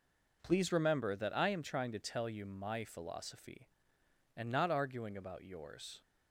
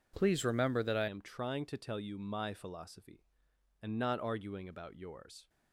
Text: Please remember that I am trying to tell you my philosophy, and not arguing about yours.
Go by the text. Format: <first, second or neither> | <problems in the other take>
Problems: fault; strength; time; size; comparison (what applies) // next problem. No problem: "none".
first | changes voice at "am"; from 1.0 s on; 4.4 s long